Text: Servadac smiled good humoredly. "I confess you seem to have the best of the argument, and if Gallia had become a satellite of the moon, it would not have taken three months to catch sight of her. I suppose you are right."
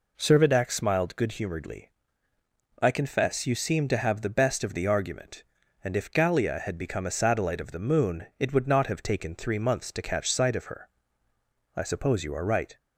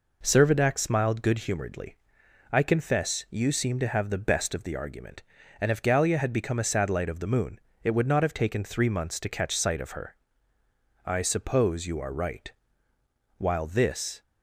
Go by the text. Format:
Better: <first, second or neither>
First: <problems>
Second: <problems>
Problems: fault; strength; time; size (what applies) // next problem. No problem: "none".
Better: first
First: none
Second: goes on to say "While this"; noticeable; from 13.3 s on; 0.84 s long